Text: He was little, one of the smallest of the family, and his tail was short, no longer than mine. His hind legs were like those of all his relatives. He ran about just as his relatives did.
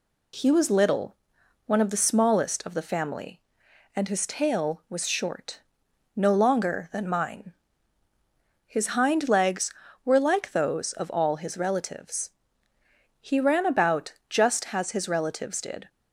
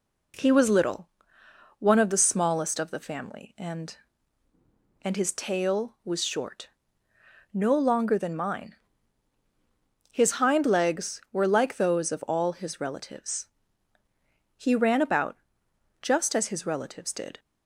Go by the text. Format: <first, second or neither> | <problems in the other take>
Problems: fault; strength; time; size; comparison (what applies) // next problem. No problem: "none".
first | says "and" twice; at 5.0 s // pauses between "about" and "just"; noticeable; at 15.3 s; 0.64 s long